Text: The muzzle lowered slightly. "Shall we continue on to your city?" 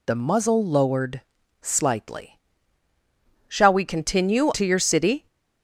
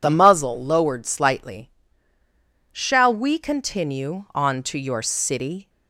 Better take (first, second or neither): second